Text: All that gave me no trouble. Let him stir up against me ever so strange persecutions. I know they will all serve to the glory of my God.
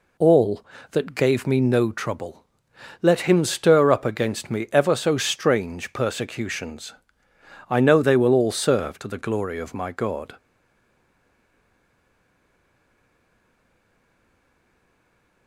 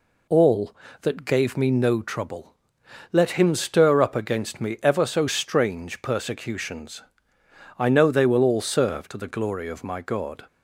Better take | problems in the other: second | stays silent after the last word; strong; from 10.3 s on; 5.1 s long

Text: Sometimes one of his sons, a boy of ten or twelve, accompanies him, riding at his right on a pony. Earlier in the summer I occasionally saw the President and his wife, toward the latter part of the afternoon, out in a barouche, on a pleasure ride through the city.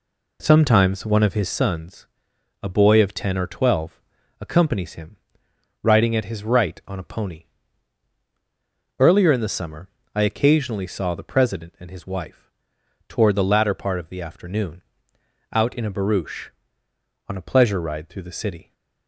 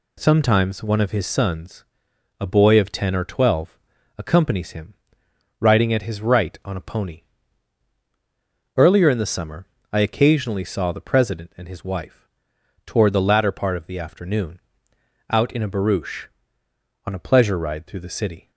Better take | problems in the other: second | starts louder than the rest; slight; until 1.6 s; 2.5 dB // pauses between "summer" and "I"; slight; at 9.9 s; 0.24 s long; slight in the second

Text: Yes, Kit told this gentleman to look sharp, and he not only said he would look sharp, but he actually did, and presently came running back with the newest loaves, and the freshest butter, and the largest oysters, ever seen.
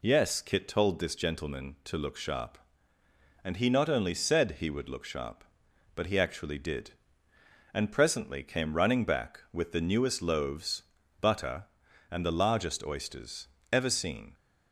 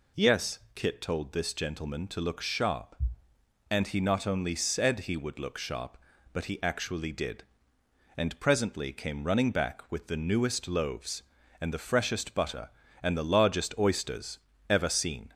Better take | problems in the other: second | skips "and the freshest"; at 11.0 s

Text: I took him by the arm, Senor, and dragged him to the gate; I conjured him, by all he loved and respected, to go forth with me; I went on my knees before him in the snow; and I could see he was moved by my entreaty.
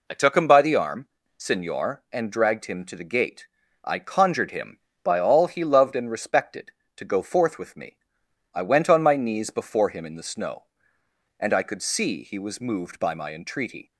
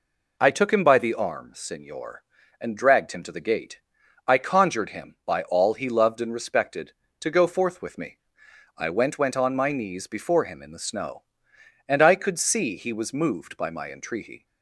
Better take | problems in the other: first | says "went" twice; at 9.1 s

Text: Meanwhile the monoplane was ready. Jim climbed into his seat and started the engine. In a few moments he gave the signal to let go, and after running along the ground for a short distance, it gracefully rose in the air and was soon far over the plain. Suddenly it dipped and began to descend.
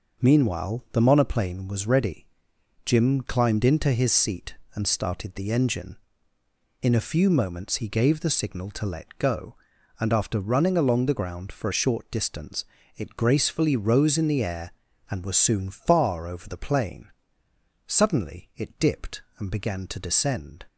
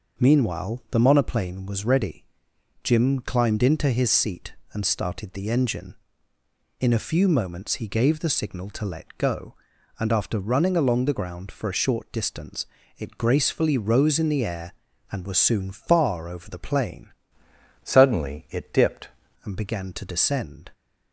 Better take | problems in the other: first | changes voice from "Suddenly" to "dipped"; from 17.8 to 19.0 s; 1.2 s long

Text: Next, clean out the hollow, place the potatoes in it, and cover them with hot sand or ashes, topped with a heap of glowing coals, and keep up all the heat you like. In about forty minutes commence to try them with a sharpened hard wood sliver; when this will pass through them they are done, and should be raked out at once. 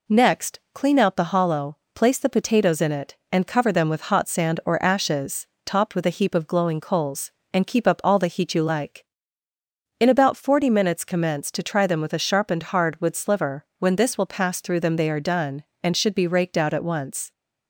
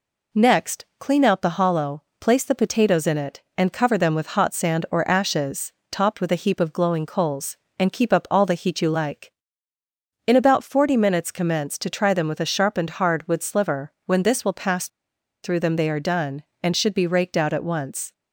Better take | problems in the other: first | pauses between "pass" and "through"; noticeable; at 14.8 s; 0.55 s long

